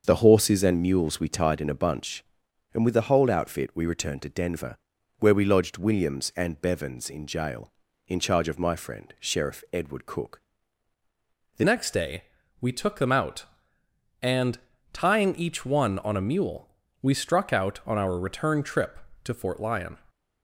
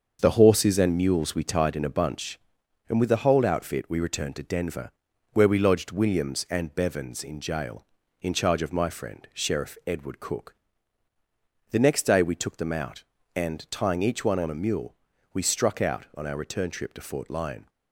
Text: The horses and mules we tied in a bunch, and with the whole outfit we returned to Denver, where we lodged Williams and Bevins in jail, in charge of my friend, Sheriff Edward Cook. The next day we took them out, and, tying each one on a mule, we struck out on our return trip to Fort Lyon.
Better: second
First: starts louder than the rest; until 1.0 s; 6.5 dB // changes voice at "next"; from 11.6 s on; 8.3 s long // pauses between "day" and "we"; slight; at 12.2 s; 0.36 s long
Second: starts louder than the rest; until 1.2 s; 6.5 dB

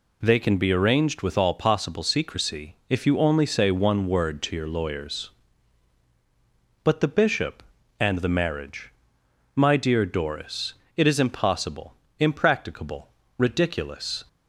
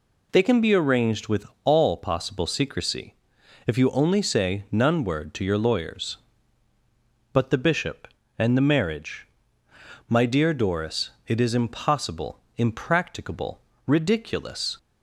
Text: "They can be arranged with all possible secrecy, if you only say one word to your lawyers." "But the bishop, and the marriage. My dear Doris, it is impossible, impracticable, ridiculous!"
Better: first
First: none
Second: pauses between "with" and "all"; slight; at 1.4 s; 0.18 s long // says "none" for "one"; at 4.6 s

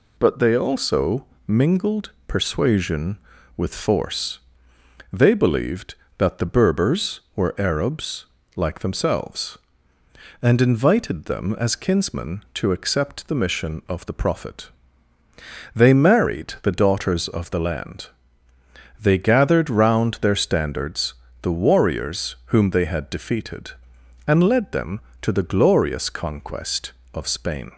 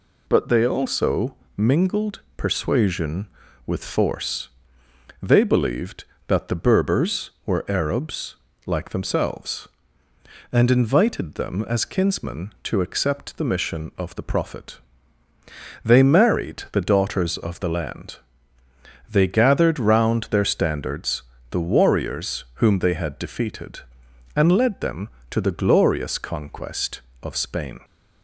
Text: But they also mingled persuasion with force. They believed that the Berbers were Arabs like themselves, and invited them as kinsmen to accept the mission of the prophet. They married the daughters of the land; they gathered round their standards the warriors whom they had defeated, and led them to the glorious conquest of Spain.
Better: neither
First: pauses between "also" and "mingled"; slight; at 1.2 s; 0.20 s long // pauses between "Arabs" and "like"; slight; at 8.2 s; 0.30 s long // pauses between "standards" and "the"; slight; at 21.1 s; 0.28 s long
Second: pauses between "also" and "mingled"; slight; at 1.3 s; 0.20 s long // pauses between "Arabs" and "like"; slight; at 8.3 s; 0.30 s long // pauses between "standards" and "the"; slight; at 21.2 s; 0.28 s long

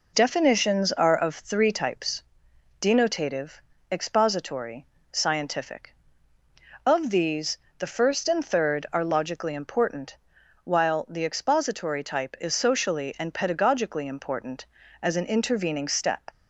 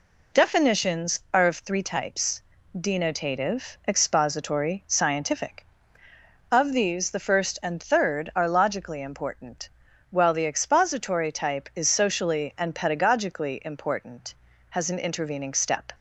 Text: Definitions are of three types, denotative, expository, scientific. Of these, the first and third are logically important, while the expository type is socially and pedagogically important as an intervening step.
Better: first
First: none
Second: says "has" for "as"; at 14.6 s

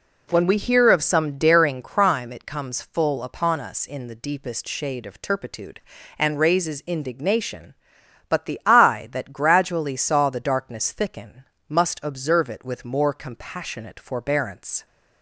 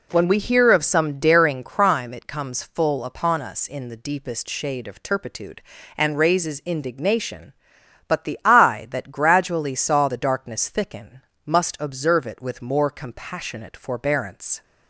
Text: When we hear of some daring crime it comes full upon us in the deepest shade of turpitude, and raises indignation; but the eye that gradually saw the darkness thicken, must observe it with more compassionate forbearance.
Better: neither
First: none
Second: none

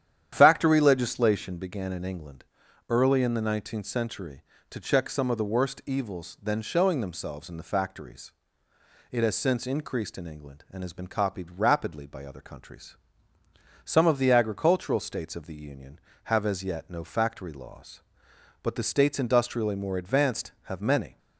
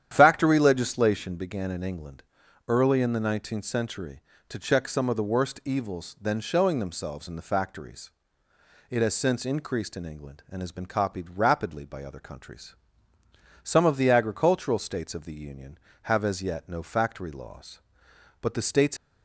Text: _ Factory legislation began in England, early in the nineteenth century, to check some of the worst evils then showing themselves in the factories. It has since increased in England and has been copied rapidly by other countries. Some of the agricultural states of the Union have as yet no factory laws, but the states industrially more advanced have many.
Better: first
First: starts louder than the rest; strong; until 1.3 s; 10 dB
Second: starts louder than the rest; strong; until 1.1 s; 10 dB // stops before "industrially more advanced have many"; at 18.9 s

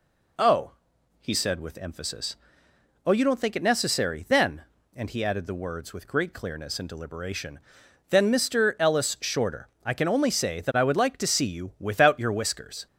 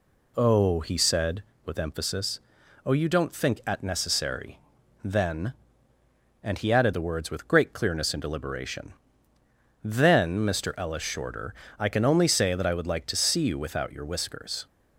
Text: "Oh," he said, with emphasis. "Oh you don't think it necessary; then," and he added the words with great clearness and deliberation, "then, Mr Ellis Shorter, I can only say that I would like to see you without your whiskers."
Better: first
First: none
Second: says "at" for "it"; at 3.6 s

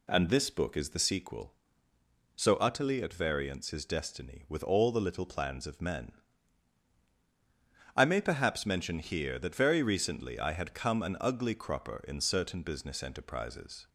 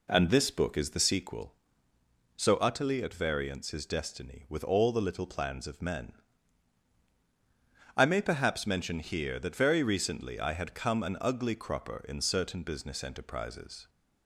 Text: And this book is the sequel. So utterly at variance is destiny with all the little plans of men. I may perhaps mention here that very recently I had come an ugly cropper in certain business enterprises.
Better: first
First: none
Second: starts louder than the rest; slight; until 1.5 s; 3.5 dB

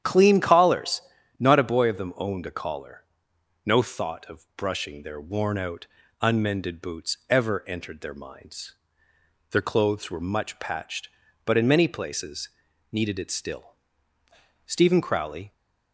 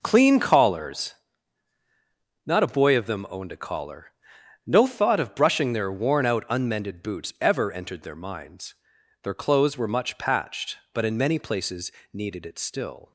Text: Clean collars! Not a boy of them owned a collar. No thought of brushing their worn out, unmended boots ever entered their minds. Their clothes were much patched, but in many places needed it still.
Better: second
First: starts louder than the rest; strong; until 1.4 s; 9.5 dB // pauses between "places" and "needed"; at 12.4 s; 0.44 s long // goes on to say "Stephen Crowley"; noticeable; from 14.6 s on; 0.86 s long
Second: pauses between "places" and "needed"; slight; at 11.9 s; 0.20 s long

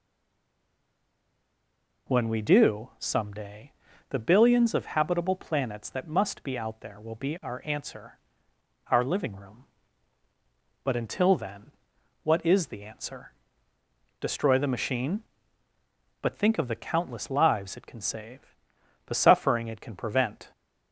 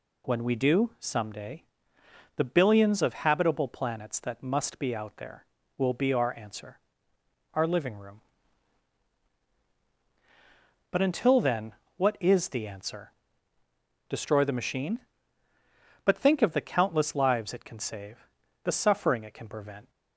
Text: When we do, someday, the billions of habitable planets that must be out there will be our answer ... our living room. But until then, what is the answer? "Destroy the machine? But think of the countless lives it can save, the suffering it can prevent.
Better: second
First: stays silent before the first word; noticeable; until 2.0 s; 2.0 s long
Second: none

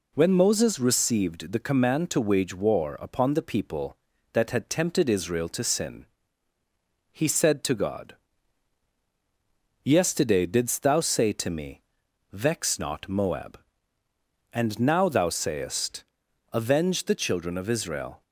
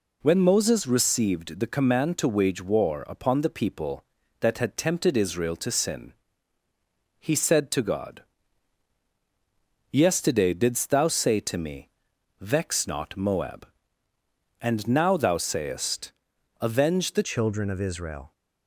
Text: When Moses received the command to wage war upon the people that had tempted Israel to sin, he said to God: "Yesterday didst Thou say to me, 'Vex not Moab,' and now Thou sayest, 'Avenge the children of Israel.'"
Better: first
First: none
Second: changes voice at "children"; from 17.2 s on; 1.1 s long

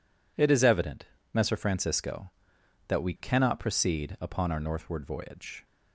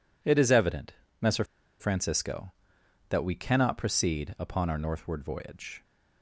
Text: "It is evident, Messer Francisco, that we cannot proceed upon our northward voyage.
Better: first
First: none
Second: pauses between "Messer" and "Francisco"; at 1.4 s; 0.36 s long

